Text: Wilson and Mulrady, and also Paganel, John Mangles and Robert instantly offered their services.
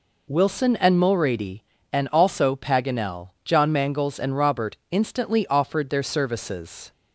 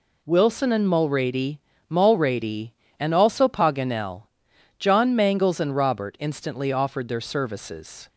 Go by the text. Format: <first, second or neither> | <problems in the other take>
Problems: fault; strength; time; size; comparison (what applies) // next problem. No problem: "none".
first | says "Mulrady" twice; at 1.9 s